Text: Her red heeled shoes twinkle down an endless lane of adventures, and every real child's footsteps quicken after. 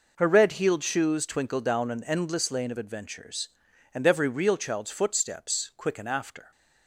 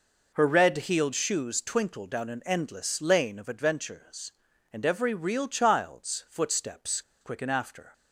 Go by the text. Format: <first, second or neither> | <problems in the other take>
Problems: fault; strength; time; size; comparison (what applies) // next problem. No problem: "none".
first | pauses between "footsteps" and "quicken"; slight; at 7.0 s; 0.19 s long